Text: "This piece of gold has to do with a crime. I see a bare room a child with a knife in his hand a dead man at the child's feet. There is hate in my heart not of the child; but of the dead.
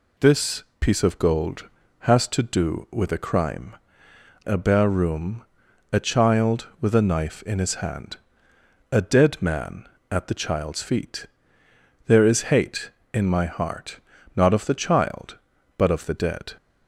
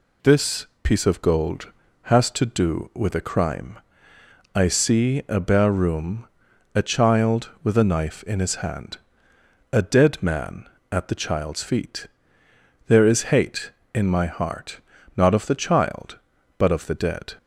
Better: second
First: pauses between "This" and "piece"; slight; at 0.6 s; 0.16 s long // skips "I see"; at 4.1 s // pauses between "room" and "a"; noticeable; at 5.4 s; 0.48 s long // pauses between "hand" and "a"; noticeable; at 8.1 s; 0.74 s long // pauses between "heart" and "not"; slight; at 13.9 s; 0.36 s long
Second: pauses between "This" and "piece"; slight; at 0.6 s; 0.16 s long // pauses between "room" and "a"; noticeable; at 6.2 s; 0.48 s long // pauses between "hand" and "a"; noticeable; at 8.9 s; 0.74 s long // pauses between "heart" and "not"; slight; at 14.7 s; 0.36 s long

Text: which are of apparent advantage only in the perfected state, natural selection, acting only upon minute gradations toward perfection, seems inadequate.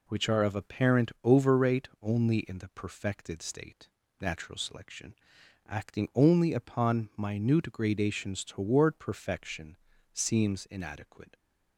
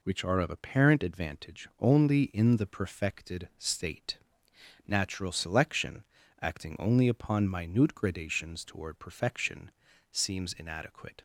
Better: second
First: says "overrate" for "advantage"; at 1.2 s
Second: none

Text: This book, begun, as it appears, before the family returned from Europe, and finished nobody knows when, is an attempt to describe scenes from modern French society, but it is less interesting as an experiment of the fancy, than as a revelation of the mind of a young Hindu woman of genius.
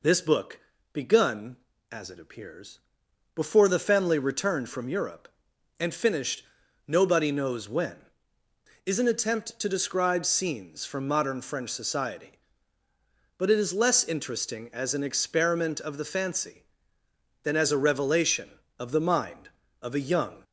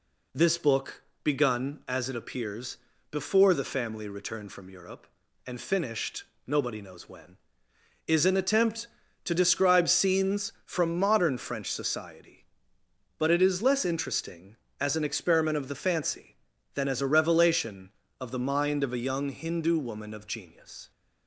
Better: second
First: pauses between "finished" and "nobody"; at 6.4 s; 0.44 s long // stops before "Hindu woman of genius"; at 20.4 s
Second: pauses between "finished" and "nobody"; slight; at 6.2 s; 0.24 s long

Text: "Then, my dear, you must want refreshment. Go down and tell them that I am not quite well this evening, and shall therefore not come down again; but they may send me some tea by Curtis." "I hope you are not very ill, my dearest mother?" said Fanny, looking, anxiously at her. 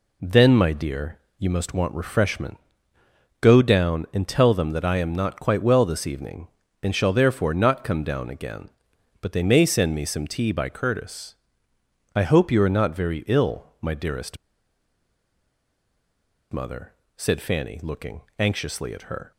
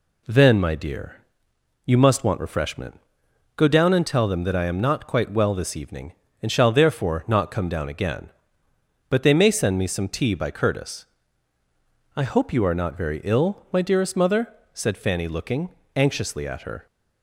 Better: second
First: pauses between "dearest" and "mother"; strong; at 14.3 s; 2.1 s long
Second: none

